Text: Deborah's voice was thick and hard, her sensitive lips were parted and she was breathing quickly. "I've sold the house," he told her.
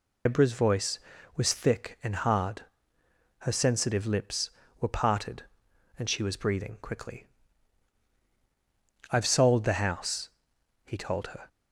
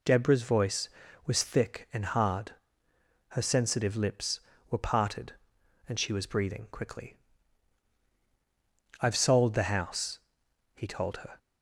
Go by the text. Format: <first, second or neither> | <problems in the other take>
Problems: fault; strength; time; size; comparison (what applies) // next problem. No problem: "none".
second | loses the start of "Deborah's"; at 0.2 s; 110 ms